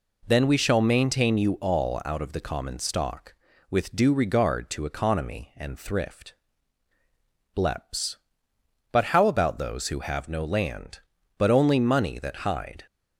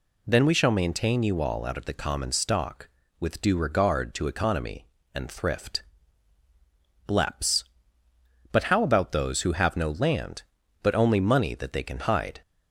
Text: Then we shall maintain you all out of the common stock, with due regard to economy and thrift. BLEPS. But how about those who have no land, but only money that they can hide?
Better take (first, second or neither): second